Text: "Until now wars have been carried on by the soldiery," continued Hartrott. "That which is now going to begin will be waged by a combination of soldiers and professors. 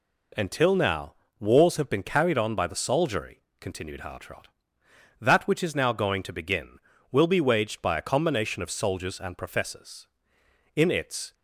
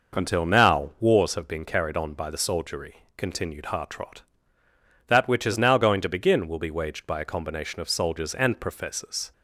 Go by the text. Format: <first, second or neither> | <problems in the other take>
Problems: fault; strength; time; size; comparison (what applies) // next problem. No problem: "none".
second | pauses between "now" and "wars"; slight; at 1.1 s; 0.26 s long // goes on to say "In its"; from 10.7 s on; 0.58 s long